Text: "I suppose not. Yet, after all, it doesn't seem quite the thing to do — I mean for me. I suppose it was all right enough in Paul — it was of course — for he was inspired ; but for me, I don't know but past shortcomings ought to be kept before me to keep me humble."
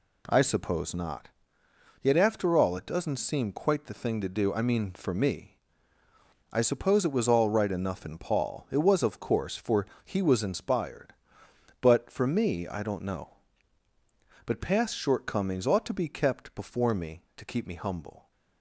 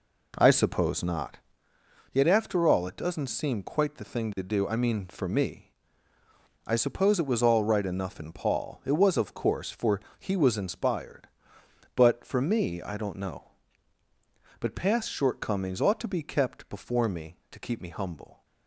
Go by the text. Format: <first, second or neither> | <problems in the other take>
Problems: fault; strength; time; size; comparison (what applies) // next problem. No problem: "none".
first | starts louder than the rest; until 1.7 s; 3.5 dB // pauses between "for" and "he"; slight; at 10.0 s; 0.18 s long; slight in the first